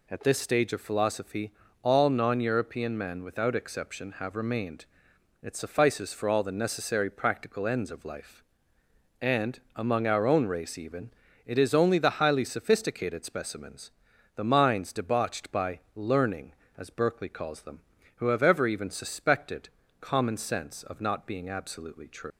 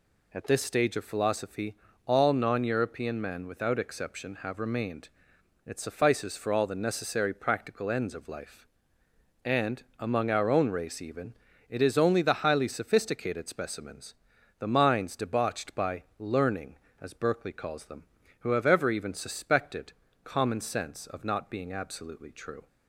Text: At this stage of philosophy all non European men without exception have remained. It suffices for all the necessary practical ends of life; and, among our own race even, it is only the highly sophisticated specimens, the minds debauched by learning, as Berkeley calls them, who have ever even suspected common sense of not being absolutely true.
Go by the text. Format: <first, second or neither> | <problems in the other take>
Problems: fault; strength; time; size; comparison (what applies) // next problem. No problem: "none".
second | pauses between "philosophy" and "all"; slight; at 1.5 s; 0.30 s long; slight in the second // pauses between "by" and "learning"; slight; at 15.7 s; 0.16 s long; slight in the second // pauses between "suspected" and "common"; slight; at 19.6 s; 0.30 s long; slight in the second // leaves "true" unfinished; at 22.3 s; 135 ms